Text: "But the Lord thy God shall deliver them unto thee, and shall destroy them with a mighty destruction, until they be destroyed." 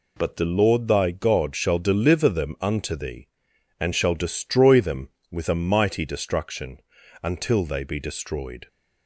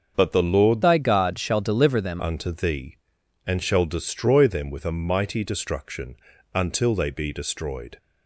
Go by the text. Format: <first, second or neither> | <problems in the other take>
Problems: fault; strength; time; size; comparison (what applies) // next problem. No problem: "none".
first | starts louder than the rest; until 1.1 s; 6.5 dB // changes voice from "thy" to "them"; from 0.8 to 2.2 s; 1.4 s long